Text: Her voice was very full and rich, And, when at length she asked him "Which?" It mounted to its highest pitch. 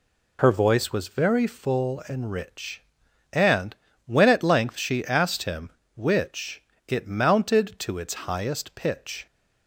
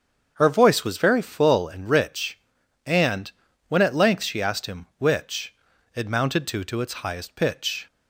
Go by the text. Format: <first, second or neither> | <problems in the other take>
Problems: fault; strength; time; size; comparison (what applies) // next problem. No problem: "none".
first | starts louder than the rest; until 1.3 s; 7 dB // says "to" twice; at 6.6 s